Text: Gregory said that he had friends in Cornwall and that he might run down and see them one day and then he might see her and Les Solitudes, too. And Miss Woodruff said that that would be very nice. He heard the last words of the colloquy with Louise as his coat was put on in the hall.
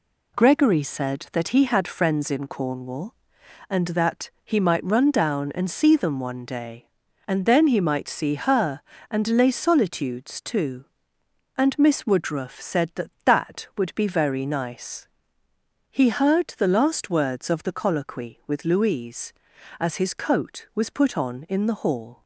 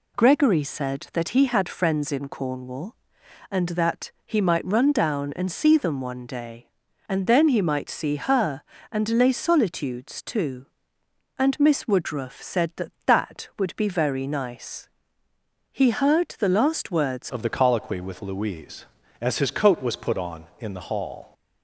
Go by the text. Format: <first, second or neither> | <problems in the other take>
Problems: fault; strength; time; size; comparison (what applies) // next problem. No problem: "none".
first | changes voice at "of"; from 17.2 s on; 4.1 s long